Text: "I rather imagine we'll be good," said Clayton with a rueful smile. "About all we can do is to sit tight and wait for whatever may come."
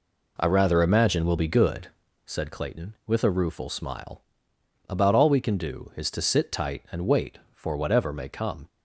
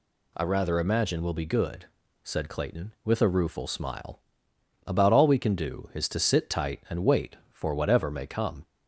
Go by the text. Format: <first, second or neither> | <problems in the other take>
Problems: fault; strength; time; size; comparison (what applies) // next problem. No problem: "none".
second | starts louder than the rest; until 2.1 s; 3.5 dB